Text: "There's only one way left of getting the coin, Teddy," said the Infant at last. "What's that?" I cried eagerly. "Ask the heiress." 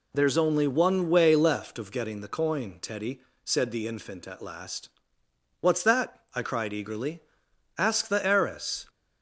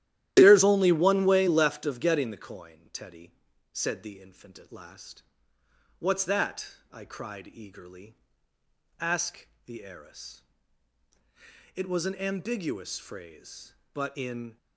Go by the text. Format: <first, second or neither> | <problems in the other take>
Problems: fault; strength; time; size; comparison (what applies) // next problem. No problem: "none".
first | starts louder than the rest; strong; until 1.3 s; 13 dB // pauses between "Ask" and "the"; slight; at 9.4 s; 0.18 s long // goes on to say "It was an ambiguous phrase but in"; strong; from 11.7 s on; 2.8 s long